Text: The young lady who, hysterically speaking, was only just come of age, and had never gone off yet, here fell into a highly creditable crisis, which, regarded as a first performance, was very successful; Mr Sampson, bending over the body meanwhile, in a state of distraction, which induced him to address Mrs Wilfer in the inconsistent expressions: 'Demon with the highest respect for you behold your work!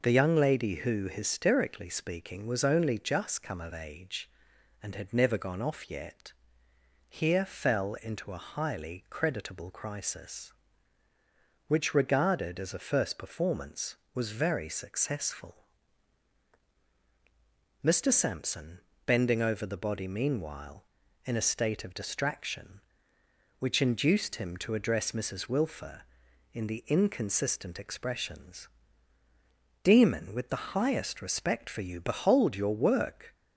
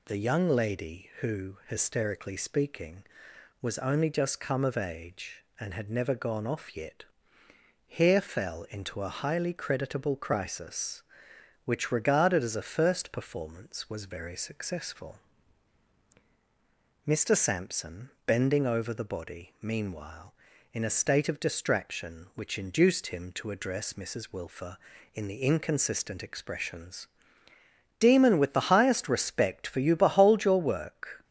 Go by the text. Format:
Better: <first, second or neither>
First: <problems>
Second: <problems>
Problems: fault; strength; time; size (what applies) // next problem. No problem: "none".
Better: neither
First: none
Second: none